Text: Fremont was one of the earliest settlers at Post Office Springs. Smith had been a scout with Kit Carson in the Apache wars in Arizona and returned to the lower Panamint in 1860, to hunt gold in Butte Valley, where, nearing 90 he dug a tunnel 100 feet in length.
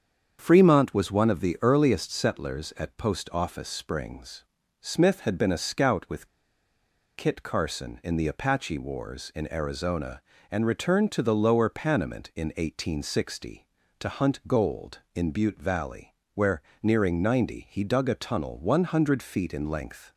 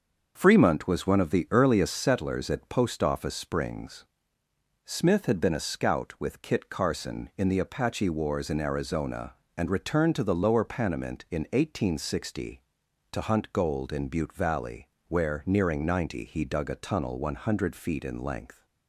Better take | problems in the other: second | starts louder than the rest; strong; until 1.4 s; 7.5 dB; also in the second // pauses between "with" and "Kit"; noticeable; at 6.2 s; 0.89 s long

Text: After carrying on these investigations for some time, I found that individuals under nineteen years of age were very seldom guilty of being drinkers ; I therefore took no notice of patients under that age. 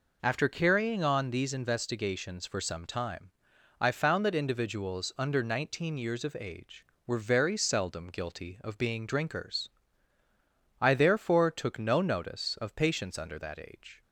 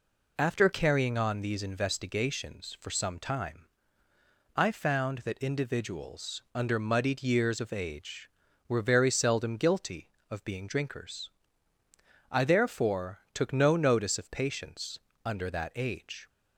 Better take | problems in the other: first | says "muddied" for "nineteen"; at 6.7 s // pauses between "patients" and "under"; slight; at 14.9 s; 0.26 s long

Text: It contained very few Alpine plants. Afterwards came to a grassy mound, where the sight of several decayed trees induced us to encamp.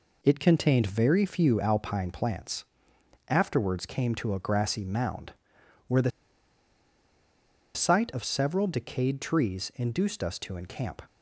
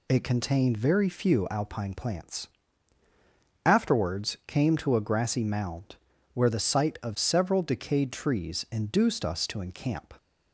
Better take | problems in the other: second | pauses between "the" and "sight"; strong; at 6.1 s; 1.6 s long

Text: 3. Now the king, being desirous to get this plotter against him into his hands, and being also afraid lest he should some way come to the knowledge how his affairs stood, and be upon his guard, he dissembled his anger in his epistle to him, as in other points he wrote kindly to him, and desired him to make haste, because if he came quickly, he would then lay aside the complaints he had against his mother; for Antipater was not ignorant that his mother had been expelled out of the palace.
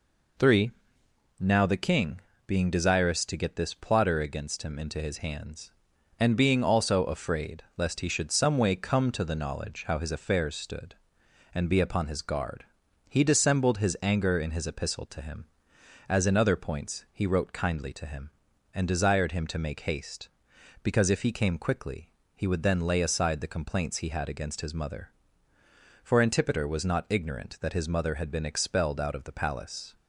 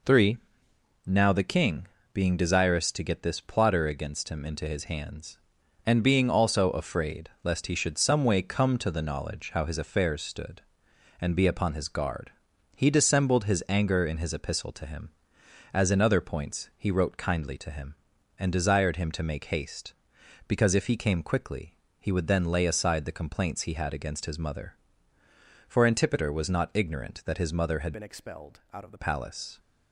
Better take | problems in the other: first | changes voice from "been" to "the"; from 27.9 to 28.9 s; 1.0 s long

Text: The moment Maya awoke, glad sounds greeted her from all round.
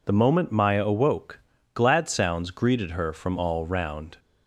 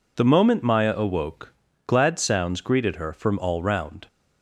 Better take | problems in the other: neither | none

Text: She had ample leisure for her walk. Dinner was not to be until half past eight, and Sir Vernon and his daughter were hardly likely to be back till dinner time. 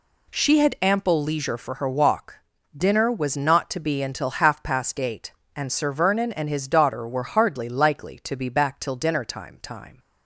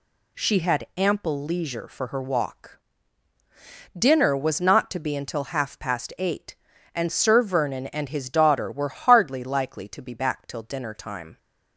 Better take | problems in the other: second | says "time" twice; at 9.6 s

